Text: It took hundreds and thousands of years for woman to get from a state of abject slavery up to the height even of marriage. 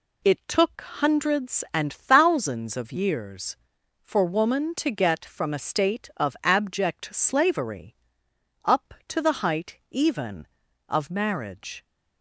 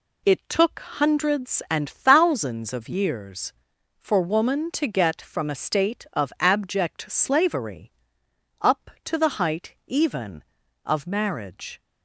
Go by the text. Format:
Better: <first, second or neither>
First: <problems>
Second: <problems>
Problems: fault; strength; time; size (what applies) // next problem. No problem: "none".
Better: neither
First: pauses between "slavery" and "up"; noticeable; at 7.9 s; 0.68 s long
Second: pauses between "slavery" and "up"; noticeable; at 7.9 s; 0.68 s long